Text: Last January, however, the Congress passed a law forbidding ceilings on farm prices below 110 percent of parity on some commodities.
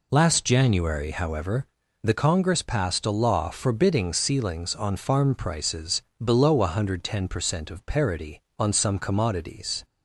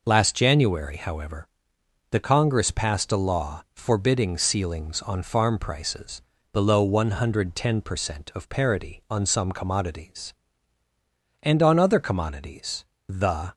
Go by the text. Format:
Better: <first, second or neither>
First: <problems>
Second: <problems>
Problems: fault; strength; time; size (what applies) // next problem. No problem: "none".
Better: first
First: pauses between "prices" and "below"; slight; at 6.0 s; 0.22 s long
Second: pauses between "prices" and "below"; slight; at 6.2 s; 0.32 s long // goes on to say "And on other commodities the"; strong; from 11.4 s on; 2.1 s long